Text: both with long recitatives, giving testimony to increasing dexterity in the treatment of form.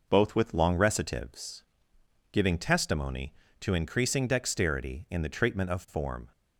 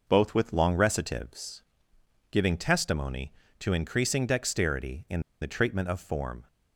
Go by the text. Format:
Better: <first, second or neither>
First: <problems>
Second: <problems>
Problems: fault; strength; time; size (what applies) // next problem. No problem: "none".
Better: first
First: none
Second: pauses between "in" and "the"; slight; at 5.1 s; 0.21 s long